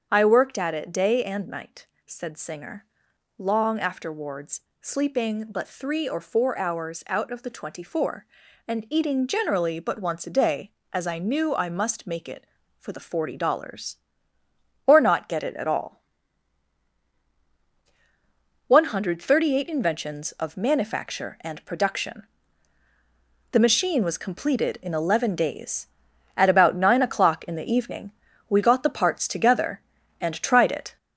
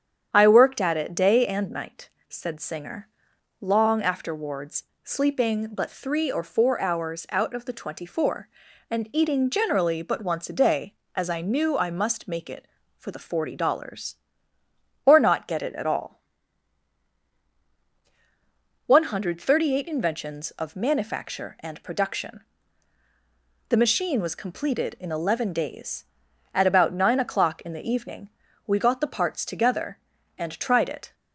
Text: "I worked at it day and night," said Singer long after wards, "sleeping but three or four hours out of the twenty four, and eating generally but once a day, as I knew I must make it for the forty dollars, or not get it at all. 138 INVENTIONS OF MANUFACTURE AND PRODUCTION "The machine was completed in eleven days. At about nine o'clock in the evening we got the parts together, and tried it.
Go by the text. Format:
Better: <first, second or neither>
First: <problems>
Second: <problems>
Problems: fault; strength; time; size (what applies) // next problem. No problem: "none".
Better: second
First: gets louder; noticeable; throughout; 4.5 dB // starts louder than the rest; strong; until 1.1 s; 7.5 dB // pauses between "Singer" and "long"; noticeable; at 2.8 s; 0.52 s long // pauses between "PRODUCTION" and "The"; strong; at 22.2 s; 1.2 s long // pauses between "evening" and "we"; at 28.1 s; 0.38 s long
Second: starts louder than the rest; strong; until 1.3 s; 8.5 dB // pauses between "Singer" and "long"; noticeable; at 3.0 s; 0.52 s long // pauses between "PRODUCTION" and "The"; strong; at 22.4 s; 1.2 s long // pauses between "evening" and "we"; at 28.2 s; 0.38 s long